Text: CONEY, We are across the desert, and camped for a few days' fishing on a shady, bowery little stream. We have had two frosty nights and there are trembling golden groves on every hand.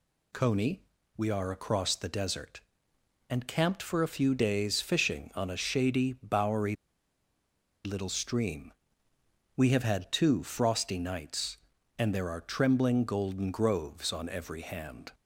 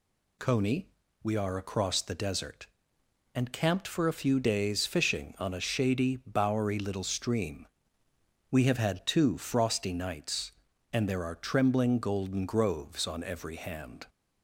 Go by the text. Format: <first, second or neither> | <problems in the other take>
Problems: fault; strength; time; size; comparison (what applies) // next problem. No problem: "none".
second | pauses between "bowery" and "little"; at 6.7 s; 1.1 s long